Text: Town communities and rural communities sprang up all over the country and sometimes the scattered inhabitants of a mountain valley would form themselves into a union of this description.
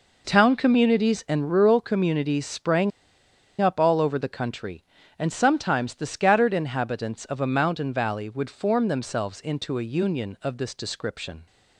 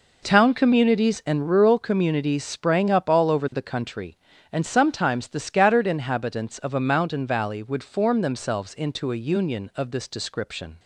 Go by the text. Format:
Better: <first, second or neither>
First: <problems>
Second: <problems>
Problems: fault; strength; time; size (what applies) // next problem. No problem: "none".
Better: second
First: pauses between "sprang" and "up"; noticeable; at 2.9 s; 0.69 s long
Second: none